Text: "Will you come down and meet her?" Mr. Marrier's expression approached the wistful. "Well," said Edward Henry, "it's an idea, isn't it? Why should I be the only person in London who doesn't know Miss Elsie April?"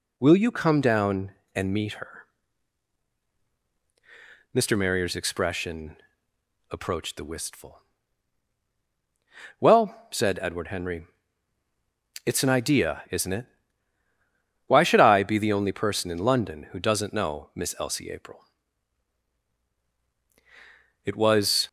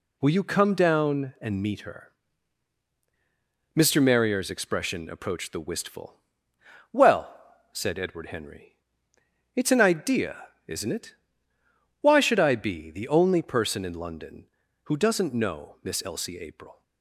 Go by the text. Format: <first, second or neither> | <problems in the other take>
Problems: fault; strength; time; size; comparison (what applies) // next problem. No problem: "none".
second | pauses between "expression" and "approached"; noticeable; at 5.9 s; 0.74 s long // goes on to say "It was"; noticeable; from 21.0 s on; 0.62 s long